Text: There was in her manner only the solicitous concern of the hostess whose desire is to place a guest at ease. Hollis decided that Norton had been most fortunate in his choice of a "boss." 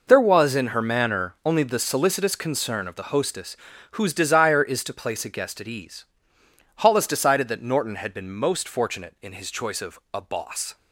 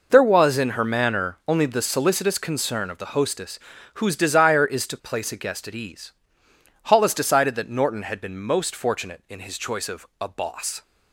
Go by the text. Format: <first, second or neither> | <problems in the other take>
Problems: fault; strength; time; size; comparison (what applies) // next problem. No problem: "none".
neither | pauses between "hostess" and "whose"; slight; the same in both